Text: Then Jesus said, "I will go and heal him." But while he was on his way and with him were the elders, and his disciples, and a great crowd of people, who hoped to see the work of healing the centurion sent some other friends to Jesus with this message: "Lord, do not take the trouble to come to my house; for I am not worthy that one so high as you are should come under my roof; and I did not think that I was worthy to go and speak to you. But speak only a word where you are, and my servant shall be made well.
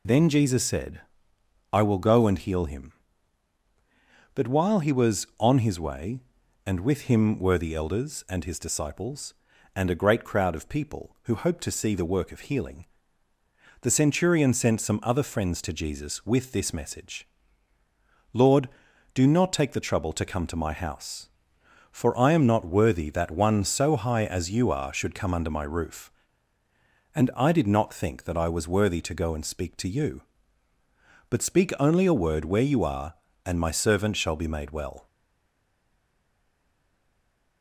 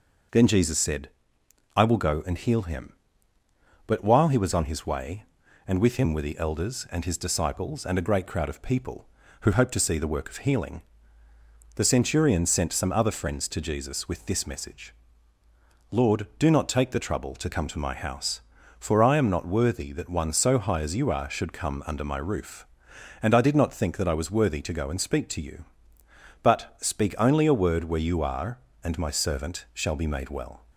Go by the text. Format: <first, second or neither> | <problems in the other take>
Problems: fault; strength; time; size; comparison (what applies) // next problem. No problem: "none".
second | pauses between "healing" and "the"; noticeable; at 12.8 s; 0.94 s long; noticeable in the second // stays silent after the last word; strong; from 35.0 s on; 2.6 s long